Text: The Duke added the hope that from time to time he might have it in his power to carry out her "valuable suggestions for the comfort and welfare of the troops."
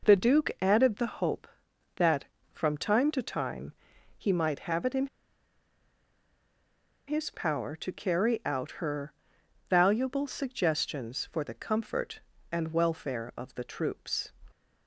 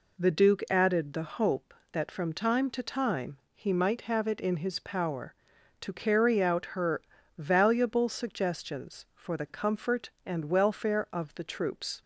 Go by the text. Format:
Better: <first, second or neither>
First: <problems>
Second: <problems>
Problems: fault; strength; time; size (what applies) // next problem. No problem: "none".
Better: second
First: pauses between "time" and "he"; noticeable; at 3.7 s; 0.46 s long // pauses between "in" and "his"; strong; at 5.0 s; 2.0 s long // pauses between "her" and "valuable"; noticeable; at 9.1 s; 0.56 s long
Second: pauses between "time" and "he"; slight; at 3.3 s; 0.16 s long // pauses between "her" and "valuable"; slight; at 7.0 s; 0.34 s long